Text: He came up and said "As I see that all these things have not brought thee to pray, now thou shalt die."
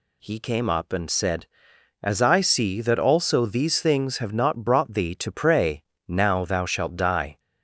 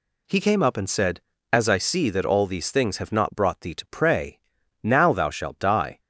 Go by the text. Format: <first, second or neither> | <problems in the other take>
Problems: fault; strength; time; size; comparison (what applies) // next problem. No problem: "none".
second | says "also" for "all"; at 2.9 s